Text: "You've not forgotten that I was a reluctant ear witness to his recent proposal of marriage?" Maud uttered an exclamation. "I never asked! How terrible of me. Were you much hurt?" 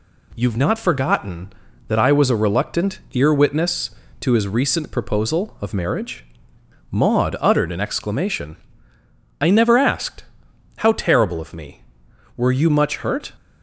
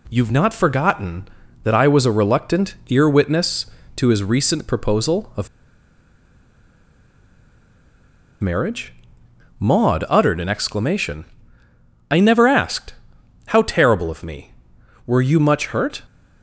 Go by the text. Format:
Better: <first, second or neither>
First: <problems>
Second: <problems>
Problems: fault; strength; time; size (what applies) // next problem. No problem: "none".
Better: first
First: none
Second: pauses between "of" and "marriage"; strong; at 5.4 s; 2.9 s long